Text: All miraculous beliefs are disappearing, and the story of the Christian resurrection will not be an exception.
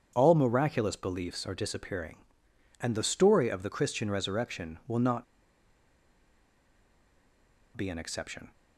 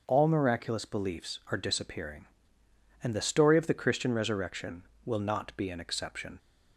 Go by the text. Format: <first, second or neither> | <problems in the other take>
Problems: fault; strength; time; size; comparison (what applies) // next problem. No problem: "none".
second | starts louder than the rest; strong; until 1.1 s; 7.5 dB; also in the second // pauses between "not" and "be"; strong; at 5.2 s; 2.5 s long